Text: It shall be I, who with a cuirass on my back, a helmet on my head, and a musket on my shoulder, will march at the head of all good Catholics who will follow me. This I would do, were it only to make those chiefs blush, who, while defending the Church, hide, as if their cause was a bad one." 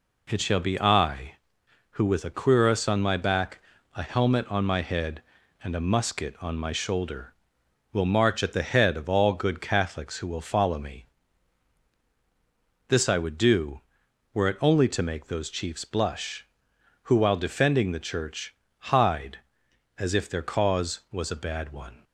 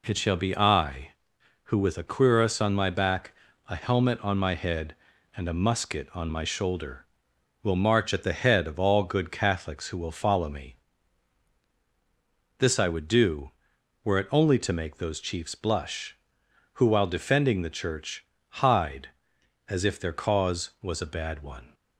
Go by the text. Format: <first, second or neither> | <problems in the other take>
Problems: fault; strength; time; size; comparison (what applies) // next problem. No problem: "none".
neither | none